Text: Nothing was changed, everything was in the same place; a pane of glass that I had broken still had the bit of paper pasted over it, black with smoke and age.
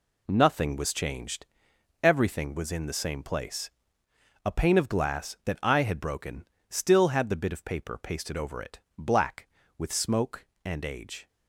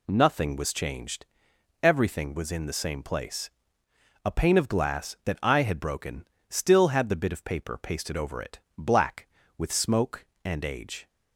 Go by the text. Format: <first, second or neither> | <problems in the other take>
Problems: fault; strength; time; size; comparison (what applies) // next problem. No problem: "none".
second | gets quieter; strong; throughout; 9 dB // pauses between "broken" and "still"; slight; at 6.4 s; 0.20 s long; slight in the second